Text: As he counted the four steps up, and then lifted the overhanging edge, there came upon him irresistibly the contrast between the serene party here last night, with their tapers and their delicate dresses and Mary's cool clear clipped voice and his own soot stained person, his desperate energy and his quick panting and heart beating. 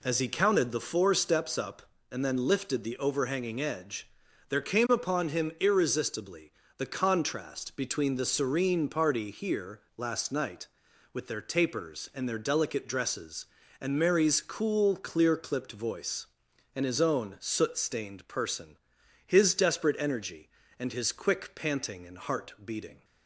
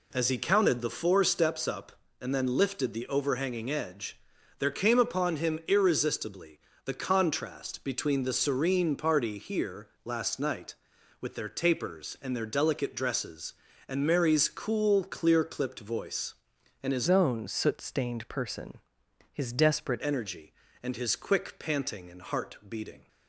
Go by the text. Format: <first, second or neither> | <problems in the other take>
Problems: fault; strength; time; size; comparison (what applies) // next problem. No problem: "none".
first | pauses between "irresistibly" and "the"; slight; at 6.5 s; 0.26 s long; slight in the first // pauses between "here" and "last"; slight; at 9.8 s; 0.16 s long; slight in the first // changes voice from "own" to "desperate"; from 17.0 to 20.0 s; 3.0 s long